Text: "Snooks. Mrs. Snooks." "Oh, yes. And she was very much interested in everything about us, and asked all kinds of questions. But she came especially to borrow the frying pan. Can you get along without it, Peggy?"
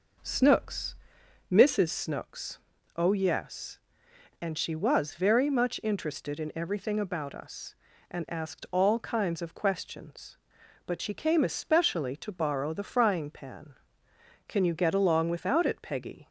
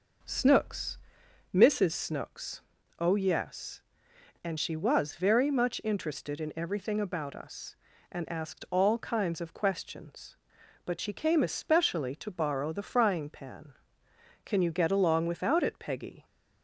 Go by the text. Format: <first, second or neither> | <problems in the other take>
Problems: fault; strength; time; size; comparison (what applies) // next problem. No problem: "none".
neither | none